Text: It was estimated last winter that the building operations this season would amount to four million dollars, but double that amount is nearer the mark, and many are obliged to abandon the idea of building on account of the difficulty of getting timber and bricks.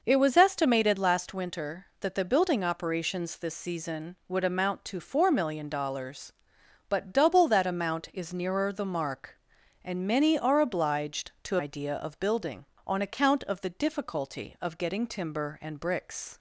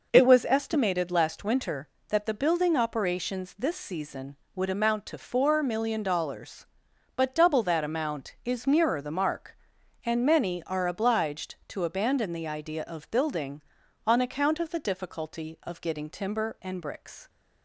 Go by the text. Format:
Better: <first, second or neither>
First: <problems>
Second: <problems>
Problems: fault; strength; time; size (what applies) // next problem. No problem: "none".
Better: second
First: skips "abandon the"; at 11.5 s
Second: none